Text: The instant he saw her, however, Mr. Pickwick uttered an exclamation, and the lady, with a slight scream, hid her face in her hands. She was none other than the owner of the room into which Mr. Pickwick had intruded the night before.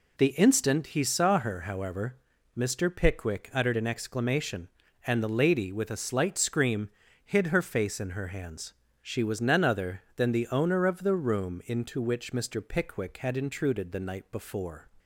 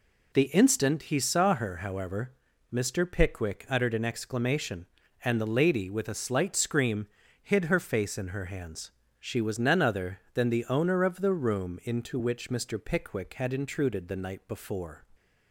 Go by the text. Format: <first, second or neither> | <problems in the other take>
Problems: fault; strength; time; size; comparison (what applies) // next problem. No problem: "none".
neither | none